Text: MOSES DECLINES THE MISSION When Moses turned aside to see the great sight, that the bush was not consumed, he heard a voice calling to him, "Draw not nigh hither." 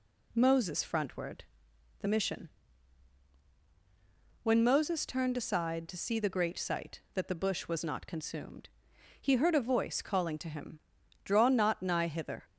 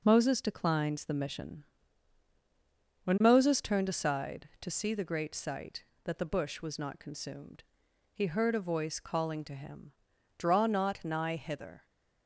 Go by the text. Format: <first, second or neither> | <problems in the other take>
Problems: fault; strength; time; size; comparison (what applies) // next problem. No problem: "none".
second | says "Frontward" for "DECLINES"; at 0.8 s // pauses between "MISSION" and "When"; strong; at 2.4 s; 1.9 s long; strong in the second